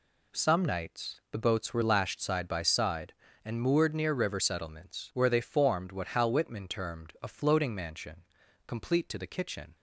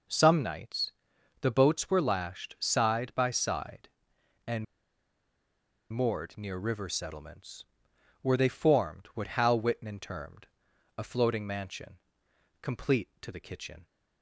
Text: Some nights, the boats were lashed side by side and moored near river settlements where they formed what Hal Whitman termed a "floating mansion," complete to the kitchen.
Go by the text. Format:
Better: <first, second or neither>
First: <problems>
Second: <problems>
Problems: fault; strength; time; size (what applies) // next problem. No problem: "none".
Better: first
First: none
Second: pauses between "and" and "moored"; strong; at 4.6 s; 1.2 s long // pauses between "settlements" and "where"; noticeable; at 7.6 s; 0.56 s long // pauses between "termed" and "a"; noticeable; at 10.4 s; 0.50 s long